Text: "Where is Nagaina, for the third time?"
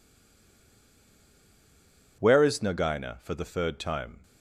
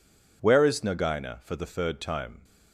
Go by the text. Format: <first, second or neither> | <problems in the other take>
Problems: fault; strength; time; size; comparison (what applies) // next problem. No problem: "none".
second | stays silent before the first word; until 2.2 s; 2.2 s long